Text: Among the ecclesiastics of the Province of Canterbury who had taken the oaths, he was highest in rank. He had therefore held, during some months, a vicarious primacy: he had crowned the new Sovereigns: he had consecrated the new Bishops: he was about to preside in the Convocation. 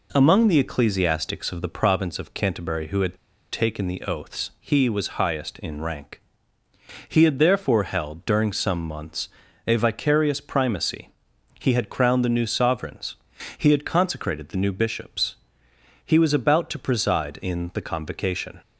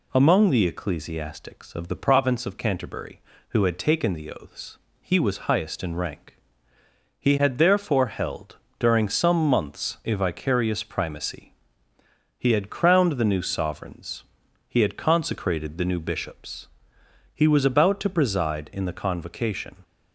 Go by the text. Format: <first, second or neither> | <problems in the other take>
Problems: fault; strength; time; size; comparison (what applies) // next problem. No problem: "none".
second | pauses between "had" and "taken"; at 3.1 s; 0.37 s long